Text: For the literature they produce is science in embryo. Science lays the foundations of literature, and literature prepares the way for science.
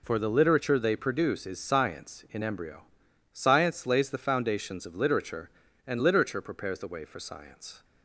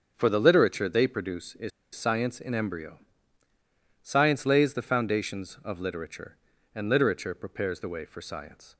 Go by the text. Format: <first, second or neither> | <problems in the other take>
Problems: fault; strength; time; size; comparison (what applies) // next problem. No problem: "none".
first | starts louder than the rest; until 1.1 s; 6.5 dB // pauses between "is" and "science"; slight; at 1.7 s; 0.25 s long